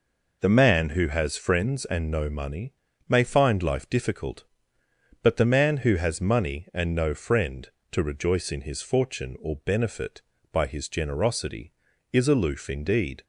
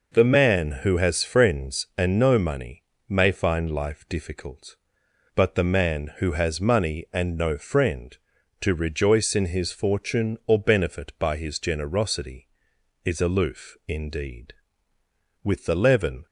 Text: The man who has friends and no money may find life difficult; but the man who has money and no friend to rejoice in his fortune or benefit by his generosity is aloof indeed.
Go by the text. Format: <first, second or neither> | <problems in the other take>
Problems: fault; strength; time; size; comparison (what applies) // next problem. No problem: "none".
first | pauses between "money" and "may"; slight; at 2.8 s; 0.24 s long; slight in the first // goes on to say "With the leaven"; noticeable; from 15.4 s on; 0.80 s long